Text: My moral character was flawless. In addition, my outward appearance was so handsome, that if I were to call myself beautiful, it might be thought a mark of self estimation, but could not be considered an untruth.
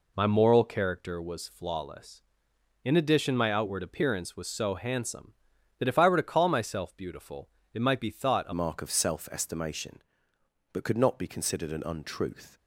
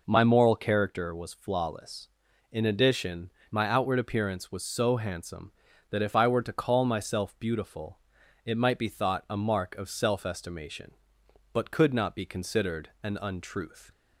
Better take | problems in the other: second | changes voice at "mark"; from 8.5 s on; 4.0 s long

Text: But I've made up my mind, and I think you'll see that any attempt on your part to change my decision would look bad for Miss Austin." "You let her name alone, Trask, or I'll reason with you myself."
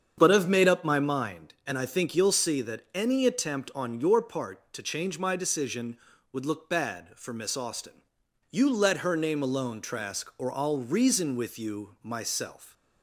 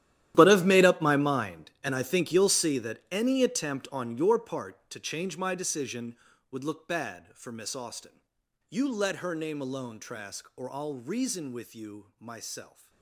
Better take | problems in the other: first | gets quieter; strong; throughout; 17.5 dB // starts louder than the rest; strong; until 1.3 s; 12.5 dB; strong in the first

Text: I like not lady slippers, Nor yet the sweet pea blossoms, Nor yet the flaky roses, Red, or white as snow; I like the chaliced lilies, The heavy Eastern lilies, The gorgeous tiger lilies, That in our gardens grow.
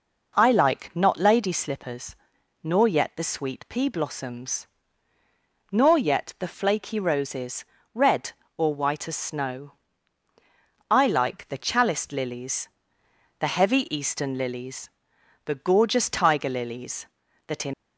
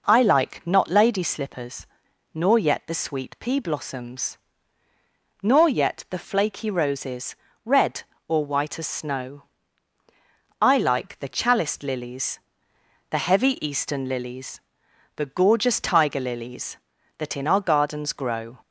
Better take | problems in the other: second | stops before "our gardens grow"; at 17.7 s

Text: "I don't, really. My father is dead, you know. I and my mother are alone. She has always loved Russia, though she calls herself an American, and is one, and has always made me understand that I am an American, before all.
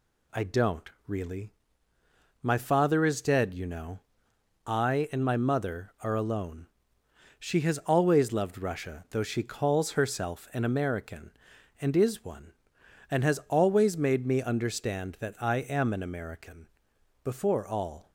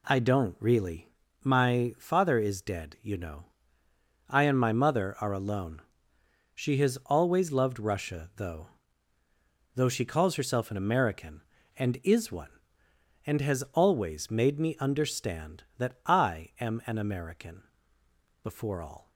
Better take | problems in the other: first | says "though" twice; at 9.7 s

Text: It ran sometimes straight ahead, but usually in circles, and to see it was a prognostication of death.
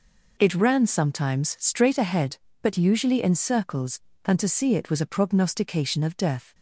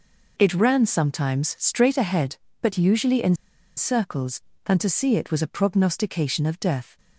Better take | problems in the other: first | pauses between "in" and "circles"; at 3.3 s; 0.42 s long

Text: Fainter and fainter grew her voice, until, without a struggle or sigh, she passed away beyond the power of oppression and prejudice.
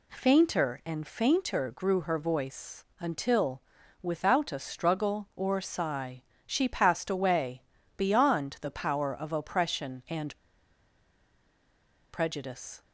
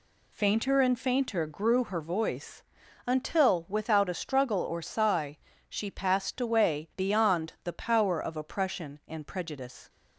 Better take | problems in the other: second | pauses between "away" and "beyond"; slight; at 7.6 s; 0.34 s long // pauses between "and" and "prejudice"; strong; at 10.3 s; 1.7 s long

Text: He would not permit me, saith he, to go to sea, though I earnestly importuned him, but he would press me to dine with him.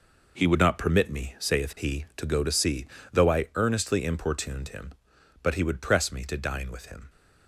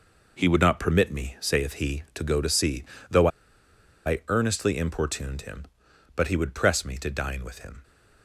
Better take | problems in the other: first | pauses between "though" and "I"; noticeable; at 3.2 s; 0.78 s long

